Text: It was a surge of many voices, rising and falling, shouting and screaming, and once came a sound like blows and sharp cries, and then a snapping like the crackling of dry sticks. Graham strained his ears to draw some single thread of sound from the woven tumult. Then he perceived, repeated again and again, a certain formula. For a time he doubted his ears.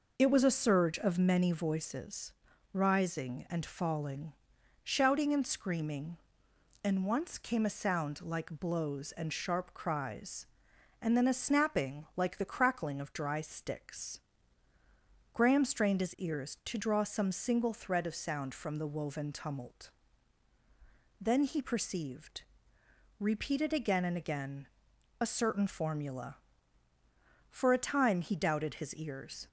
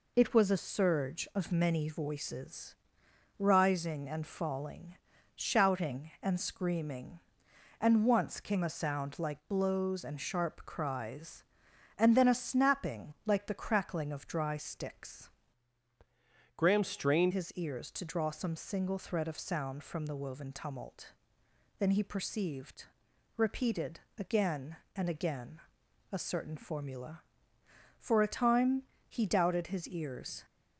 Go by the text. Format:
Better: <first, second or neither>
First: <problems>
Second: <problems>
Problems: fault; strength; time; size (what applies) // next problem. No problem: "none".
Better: first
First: none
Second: changes voice from "Graham" to "strained"; from 16.5 to 17.3 s; 0.8 s long // pauses between "repeated" and "again"; slight; at 23.9 s; 0.18 s long // pauses between "time" and "he"; slight; at 28.8 s; 0.26 s long